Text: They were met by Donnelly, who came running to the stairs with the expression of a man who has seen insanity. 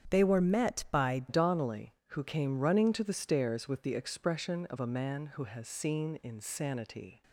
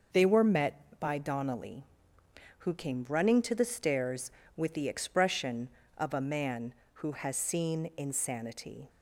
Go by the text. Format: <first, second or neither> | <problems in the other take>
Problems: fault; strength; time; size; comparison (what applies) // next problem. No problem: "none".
second | starts louder than the rest; strong; until 1.1 s; 9 dB // changes voice at "Donnelly"; from 1.2 s on; 6.0 s long